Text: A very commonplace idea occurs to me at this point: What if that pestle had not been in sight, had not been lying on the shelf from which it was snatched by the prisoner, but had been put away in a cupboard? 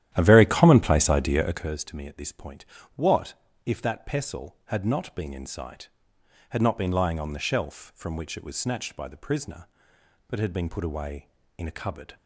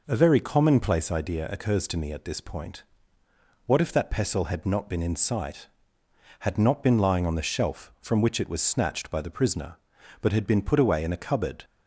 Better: second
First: starts louder than the rest; strong; until 1.7 s; 12 dB // pauses between "What" and "if"; slight; at 3.3 s; 0.32 s long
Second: none

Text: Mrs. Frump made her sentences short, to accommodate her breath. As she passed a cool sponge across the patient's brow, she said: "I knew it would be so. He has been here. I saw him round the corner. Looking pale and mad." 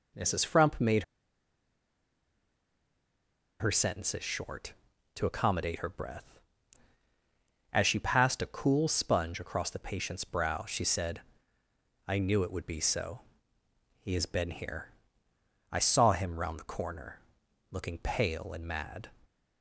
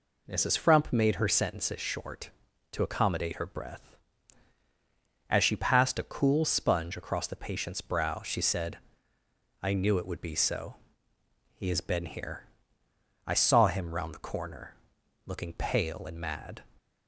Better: second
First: pauses between "made" and "her"; strong; at 1.0 s; 2.5 s long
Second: none

